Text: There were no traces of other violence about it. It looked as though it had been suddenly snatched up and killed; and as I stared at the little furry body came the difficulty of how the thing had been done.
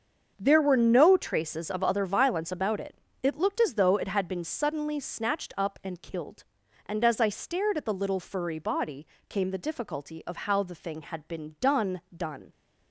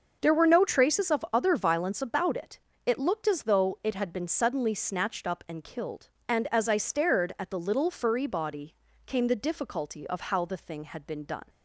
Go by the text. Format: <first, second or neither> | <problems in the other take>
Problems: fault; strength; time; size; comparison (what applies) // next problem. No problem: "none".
second | starts louder than the rest; until 1.3 s; 7 dB; also in the second // pauses between "body" and "came"; slight; at 9.0 s; 0.22 s long; slight in the second // says "done" twice; at 12.1 s